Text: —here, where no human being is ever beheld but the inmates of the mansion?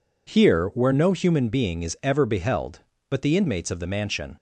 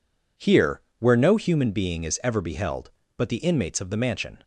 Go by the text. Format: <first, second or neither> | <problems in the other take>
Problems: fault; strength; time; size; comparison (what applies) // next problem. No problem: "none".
neither | none